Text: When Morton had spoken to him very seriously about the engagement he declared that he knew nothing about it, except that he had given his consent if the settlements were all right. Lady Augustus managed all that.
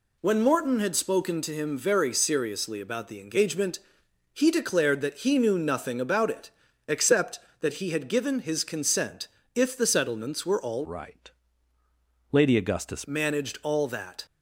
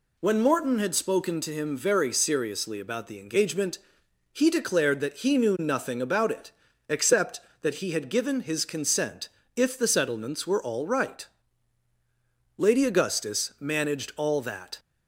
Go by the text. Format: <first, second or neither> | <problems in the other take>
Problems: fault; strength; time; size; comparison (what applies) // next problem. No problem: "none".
second | pauses between "engagement" and "he"; noticeable; at 3.7 s; 0.56 s long; noticeable in the second // pauses between "consent" and "if"; slight; at 9.2 s; 0.30 s long; slight in the second // changes voice from "right" to "Augustus"; from 10.8 to 13.0 s; 2.2 s long